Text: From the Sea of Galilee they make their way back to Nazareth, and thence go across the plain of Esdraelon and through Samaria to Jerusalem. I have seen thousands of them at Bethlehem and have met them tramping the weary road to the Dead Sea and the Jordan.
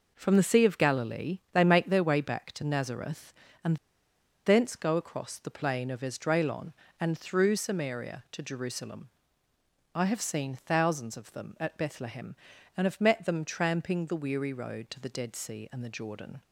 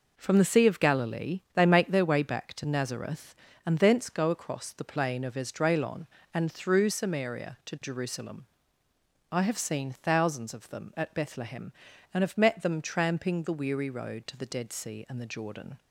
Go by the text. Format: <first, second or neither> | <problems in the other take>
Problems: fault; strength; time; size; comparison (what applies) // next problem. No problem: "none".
second | pauses between "and" and "thence"; noticeable; at 3.7 s; 0.70 s long